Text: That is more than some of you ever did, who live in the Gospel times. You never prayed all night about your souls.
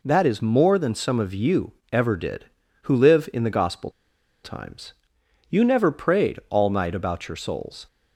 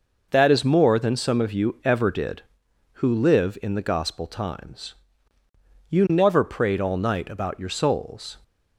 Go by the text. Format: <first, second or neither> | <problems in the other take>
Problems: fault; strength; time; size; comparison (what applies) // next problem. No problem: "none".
second | pauses between "you" and "ever"; slight; at 1.7 s; 0.18 s long // pauses between "Gospel" and "times"; noticeable; at 3.9 s; 0.51 s long